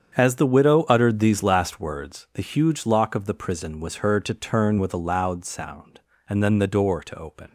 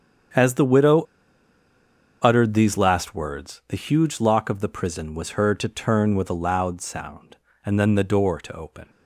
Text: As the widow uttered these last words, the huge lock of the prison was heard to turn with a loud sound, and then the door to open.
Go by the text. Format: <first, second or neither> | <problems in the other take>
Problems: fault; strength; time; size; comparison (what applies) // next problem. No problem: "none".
first | starts louder than the rest; strong; until 2.5 s; 8 dB; strong in the first // pauses between "widow" and "uttered"; at 1.0 s; 1.1 s long